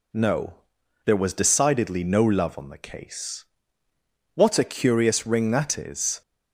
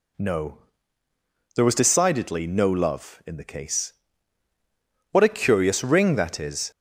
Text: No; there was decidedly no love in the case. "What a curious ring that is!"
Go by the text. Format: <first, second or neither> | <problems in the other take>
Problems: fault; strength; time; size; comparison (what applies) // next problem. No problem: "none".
second | says "on" for "in"; at 2.5 s